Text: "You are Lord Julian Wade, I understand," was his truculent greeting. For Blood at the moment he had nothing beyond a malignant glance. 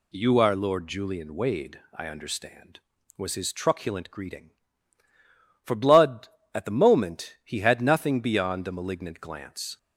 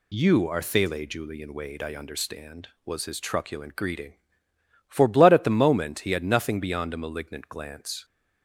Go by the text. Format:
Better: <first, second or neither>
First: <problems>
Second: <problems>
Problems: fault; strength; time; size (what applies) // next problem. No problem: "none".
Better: first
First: none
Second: says "Thele" for "Lord"; at 0.6 s